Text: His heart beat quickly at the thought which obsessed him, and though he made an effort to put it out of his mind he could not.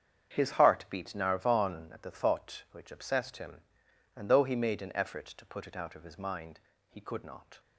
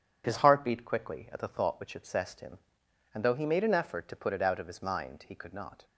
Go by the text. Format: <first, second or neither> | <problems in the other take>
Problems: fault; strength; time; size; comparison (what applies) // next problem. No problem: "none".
second | starts louder than the rest; strong; until 1.3 s; 8 dB // says "narvon" for "quickly"; at 1.0 s // pauses between "mind" and "he"; slight; at 6.5 s; 0.30 s long